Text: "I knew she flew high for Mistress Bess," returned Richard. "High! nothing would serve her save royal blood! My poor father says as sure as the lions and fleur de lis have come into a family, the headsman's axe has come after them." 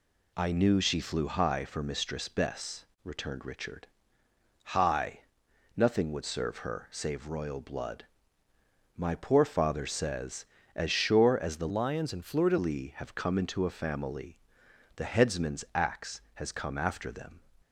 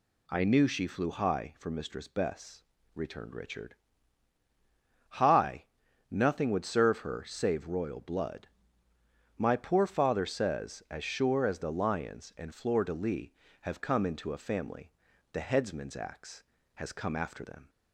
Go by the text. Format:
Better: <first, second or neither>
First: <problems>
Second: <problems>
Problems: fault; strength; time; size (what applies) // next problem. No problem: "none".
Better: second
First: changes voice from "lions" to "de"; from 11.6 to 12.5 s; 0.9 s long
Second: none